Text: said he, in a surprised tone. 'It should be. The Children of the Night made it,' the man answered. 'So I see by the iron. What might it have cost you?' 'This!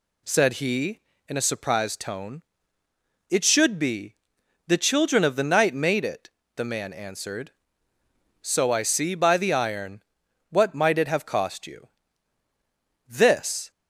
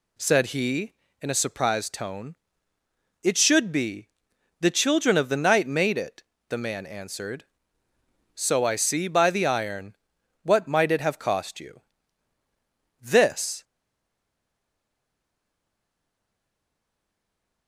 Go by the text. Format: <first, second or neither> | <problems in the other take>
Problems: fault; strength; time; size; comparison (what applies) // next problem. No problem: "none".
first | stays silent after the last word; strong; from 13.6 s on; 4.0 s long